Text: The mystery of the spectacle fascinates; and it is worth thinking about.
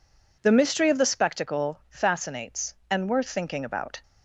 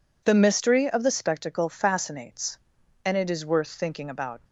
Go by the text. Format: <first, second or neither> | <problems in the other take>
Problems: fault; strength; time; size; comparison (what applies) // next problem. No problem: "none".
second | skips "it is"; at 3.0 s